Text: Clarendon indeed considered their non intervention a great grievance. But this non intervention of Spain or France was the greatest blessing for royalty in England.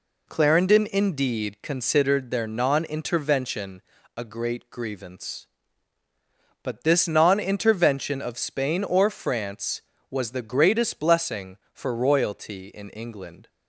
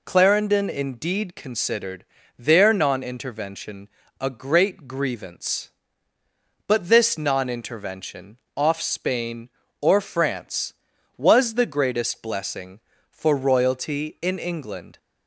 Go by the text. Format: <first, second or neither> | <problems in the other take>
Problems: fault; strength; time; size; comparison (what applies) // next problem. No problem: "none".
first | pauses between "considered" and "their"; slight; at 2.0 s; 0.34 s long // pauses between "intervention" and "a"; slight; at 3.8 s; 0.32 s long; slight in the first // says "off" for "of"; at 8.5 s